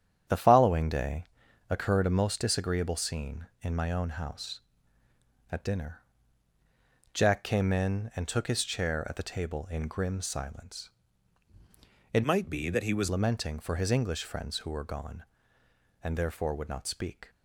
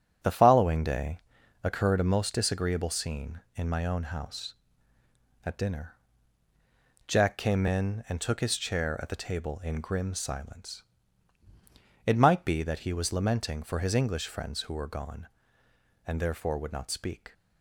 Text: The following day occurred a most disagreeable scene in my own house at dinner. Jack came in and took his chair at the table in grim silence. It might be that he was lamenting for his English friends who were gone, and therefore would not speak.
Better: second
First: starts louder than the rest; strong; until 1.7 s; 9.5 dB // pauses between "day" and "occurred"; noticeable; at 1.2 s; 0.46 s long // changes voice from "might" to "was"; from 12.2 to 13.0 s; 0.8 s long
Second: starts louder than the rest; strong; until 1.7 s; 9 dB // pauses between "day" and "occurred"; noticeable; at 1.1 s; 0.46 s long

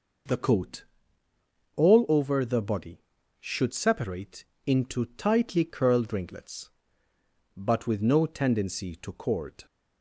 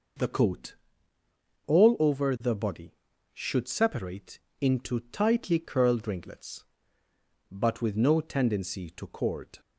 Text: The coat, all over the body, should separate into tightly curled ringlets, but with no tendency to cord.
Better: neither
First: pauses between "separate" and "into"; slight; at 4.4 s; 0.22 s long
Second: pauses between "separate" and "into"; slight; at 4.3 s; 0.22 s long

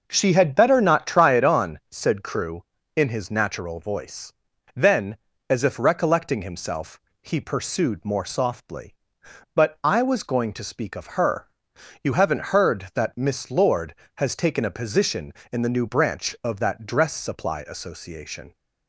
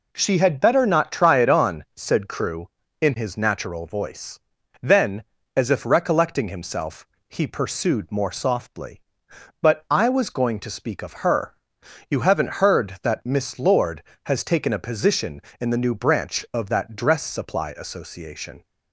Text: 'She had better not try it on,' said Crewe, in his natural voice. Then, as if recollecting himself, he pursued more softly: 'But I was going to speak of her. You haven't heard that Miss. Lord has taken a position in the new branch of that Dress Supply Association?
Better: second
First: starts louder than the rest; noticeable; until 1.4 s; 5.5 dB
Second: none

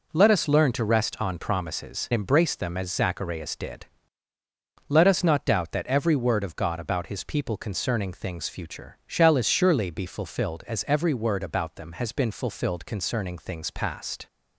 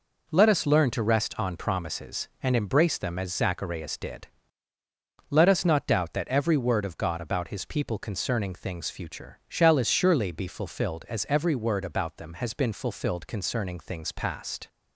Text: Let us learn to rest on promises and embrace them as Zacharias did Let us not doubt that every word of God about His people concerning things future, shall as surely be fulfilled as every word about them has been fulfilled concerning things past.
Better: second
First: skips "and"; at 2.1 s // pauses between "did" and "Let"; at 3.8 s; 1.0 s long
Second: pauses between "did" and "Let"; at 4.2 s; 1.0 s long

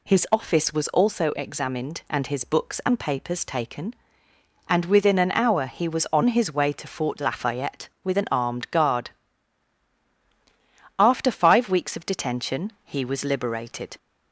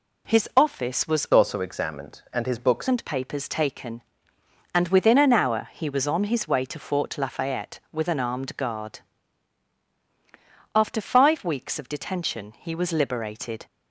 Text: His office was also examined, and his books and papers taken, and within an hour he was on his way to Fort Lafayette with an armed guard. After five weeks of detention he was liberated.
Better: first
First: none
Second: changes voice from "also" to "books"; from 1.3 to 2.8 s; 1.5 s long

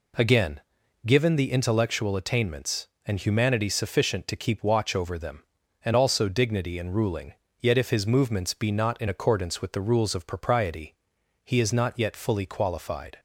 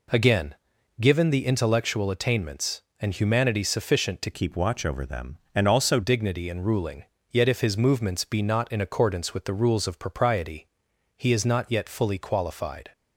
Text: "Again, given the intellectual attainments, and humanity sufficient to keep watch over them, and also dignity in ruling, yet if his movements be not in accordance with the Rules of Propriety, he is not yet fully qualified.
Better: first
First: none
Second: changes voice from "keep" to "also"; from 4.3 to 6.0 s; 1.7 s long

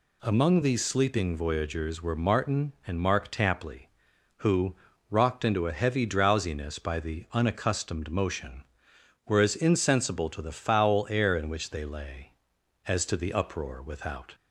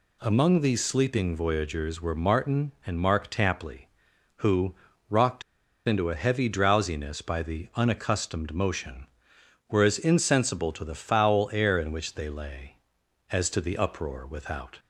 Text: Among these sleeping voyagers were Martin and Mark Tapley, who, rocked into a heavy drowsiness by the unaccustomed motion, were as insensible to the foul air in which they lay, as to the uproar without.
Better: first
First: none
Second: pauses between "rocked" and "into"; at 5.4 s; 0.45 s long

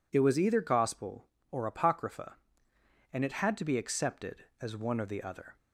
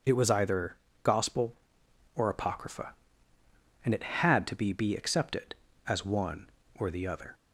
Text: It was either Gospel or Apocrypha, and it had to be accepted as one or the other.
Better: first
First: none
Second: pauses between "either" and "Gospel"; slight; at 0.7 s; 0.26 s long // says "be" twice; at 4.7 s

